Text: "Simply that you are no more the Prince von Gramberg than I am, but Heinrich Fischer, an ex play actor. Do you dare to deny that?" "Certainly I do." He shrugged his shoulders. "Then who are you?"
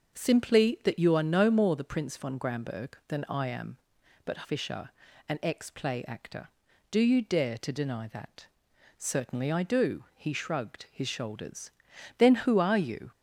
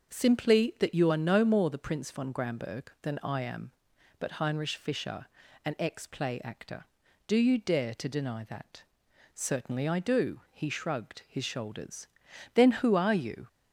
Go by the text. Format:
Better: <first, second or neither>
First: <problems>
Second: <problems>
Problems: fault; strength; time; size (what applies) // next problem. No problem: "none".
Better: second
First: starts louder than the rest; until 1.2 s; 6.5 dB // skips "Heinrich"; at 4.4 s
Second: starts louder than the rest; noticeable; until 1.1 s; 6 dB